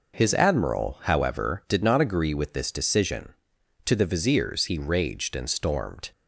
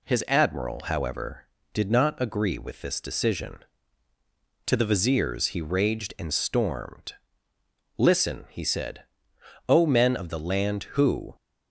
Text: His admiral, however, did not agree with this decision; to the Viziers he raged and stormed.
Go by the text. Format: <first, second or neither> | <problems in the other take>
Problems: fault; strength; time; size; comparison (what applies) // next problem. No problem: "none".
first | goes on to say "Listen he said O men of the land who"; strong; from 7.9 s on; 3.3 s long